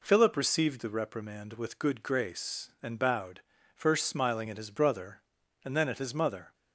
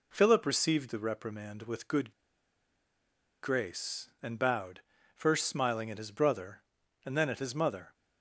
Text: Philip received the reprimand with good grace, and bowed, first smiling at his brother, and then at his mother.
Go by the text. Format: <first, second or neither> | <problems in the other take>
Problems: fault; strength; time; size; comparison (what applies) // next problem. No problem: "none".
first | pauses between "good" and "grace"; strong; at 2.1 s; 1.3 s long